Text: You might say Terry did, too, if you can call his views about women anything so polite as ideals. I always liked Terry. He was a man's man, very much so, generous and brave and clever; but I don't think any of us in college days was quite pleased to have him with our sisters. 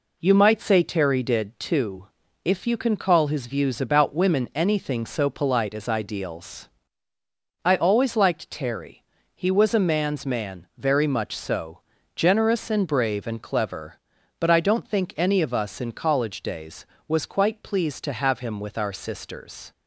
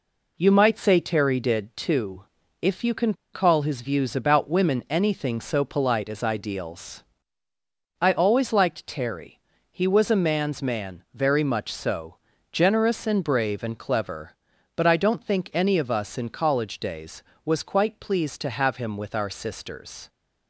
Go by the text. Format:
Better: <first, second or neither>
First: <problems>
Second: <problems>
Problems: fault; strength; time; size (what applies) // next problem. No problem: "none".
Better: first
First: none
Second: pauses between "can" and "call"; slight; at 3.1 s; 0.20 s long